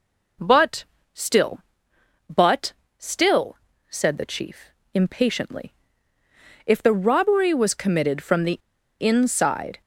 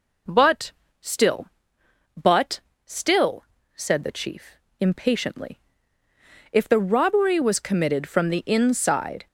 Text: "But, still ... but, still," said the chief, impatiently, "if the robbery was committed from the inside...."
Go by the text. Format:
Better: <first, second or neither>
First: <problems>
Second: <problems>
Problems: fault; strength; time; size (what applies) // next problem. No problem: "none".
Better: second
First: pauses between "the" and "inside"; at 8.5 s; 0.43 s long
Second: none